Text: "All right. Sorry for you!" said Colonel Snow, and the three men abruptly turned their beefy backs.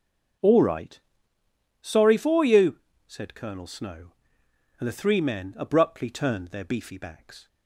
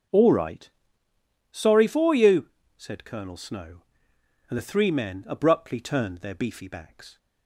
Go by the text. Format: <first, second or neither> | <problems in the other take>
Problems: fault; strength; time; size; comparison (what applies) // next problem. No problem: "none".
neither | starts louder than the rest; the same in both